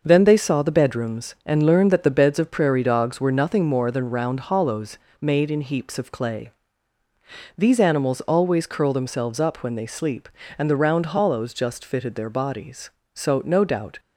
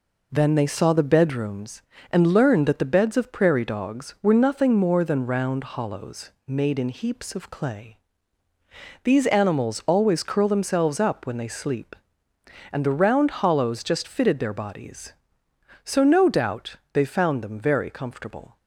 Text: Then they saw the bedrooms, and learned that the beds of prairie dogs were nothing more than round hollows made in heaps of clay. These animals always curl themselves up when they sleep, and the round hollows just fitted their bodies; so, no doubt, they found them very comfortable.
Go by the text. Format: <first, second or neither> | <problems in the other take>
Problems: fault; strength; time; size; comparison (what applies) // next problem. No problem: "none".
second | pauses between "hollows" and "made"; slight; at 4.9 s; 0.24 s long; slight in the second // stops before "they found them very comfortable"; at 13.9 s